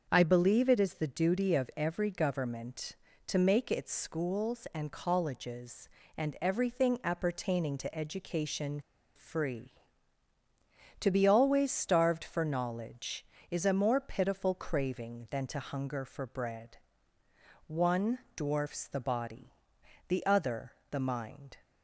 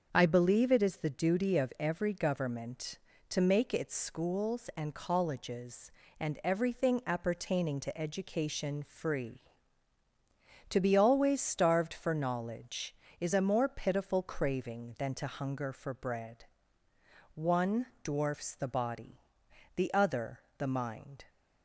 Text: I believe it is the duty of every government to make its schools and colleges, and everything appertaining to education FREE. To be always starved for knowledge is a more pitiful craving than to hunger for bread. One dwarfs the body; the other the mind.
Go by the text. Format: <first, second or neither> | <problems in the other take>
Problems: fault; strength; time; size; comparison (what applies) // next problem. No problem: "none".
second | starts louder than the rest; until 1.1 s; 6.5 dB; also in the second // pauses between "education" and "FREE"; slight; at 8.8 s; 0.35 s long // pauses between "One" and "dwarfs"; slight; at 18.1 s; 0.18 s long; slight in the second // pauses between "other" and "the"; slight; at 20.7 s; 0.18 s long; slight in the second